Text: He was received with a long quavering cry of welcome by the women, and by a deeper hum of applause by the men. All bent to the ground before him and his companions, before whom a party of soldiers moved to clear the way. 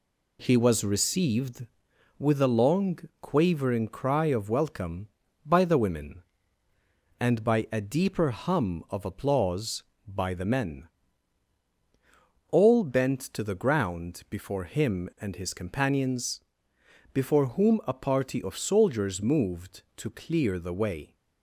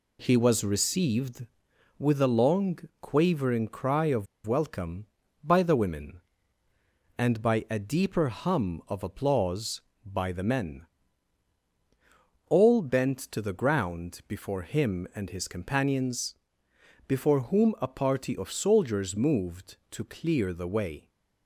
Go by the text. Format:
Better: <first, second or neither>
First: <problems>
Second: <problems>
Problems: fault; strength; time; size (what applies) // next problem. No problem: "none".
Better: first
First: pauses between "long" and "quavering"; slight; at 2.9 s; 0.22 s long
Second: pauses between "long" and "quavering"; slight; at 2.7 s; 0.22 s long // pauses between "of" and "welcome"; slight; at 4.2 s; 0.20 s long